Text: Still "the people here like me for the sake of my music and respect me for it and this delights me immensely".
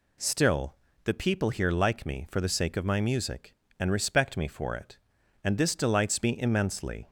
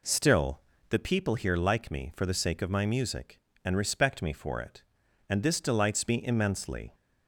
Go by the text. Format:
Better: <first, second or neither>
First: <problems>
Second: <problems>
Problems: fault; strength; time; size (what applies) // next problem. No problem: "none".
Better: first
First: pauses between "Still" and "the"; slight; at 0.7 s; 0.30 s long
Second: starts louder than the rest; slight; until 1.2 s; 3 dB // pauses between "Still" and "the"; slight; at 0.6 s; 0.30 s long